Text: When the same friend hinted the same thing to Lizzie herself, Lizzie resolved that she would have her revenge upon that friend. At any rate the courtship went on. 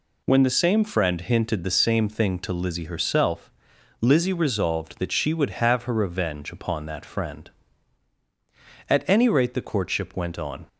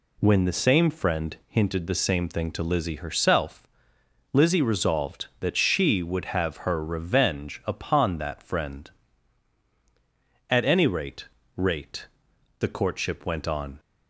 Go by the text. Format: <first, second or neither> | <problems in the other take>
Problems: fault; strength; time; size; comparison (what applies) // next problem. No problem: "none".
first | says "rate" twice; at 11.5 s